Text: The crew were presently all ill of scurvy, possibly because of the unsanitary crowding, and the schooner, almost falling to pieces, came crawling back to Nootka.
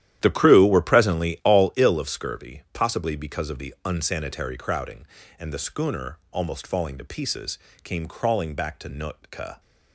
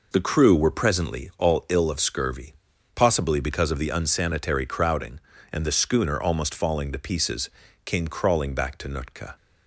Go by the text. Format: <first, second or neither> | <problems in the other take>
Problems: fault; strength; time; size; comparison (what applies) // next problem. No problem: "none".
second | starts louder than the rest; strong; until 1.7 s; 11.5 dB